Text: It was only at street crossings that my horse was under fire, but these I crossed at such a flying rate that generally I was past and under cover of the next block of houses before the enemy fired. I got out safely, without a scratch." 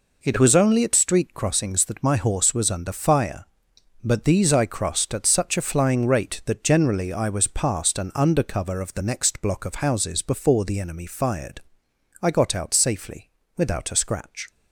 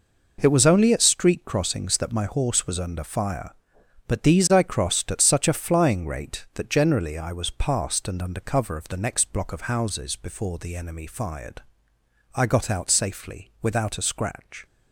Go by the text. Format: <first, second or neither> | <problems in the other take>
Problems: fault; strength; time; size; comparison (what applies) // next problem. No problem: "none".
neither | none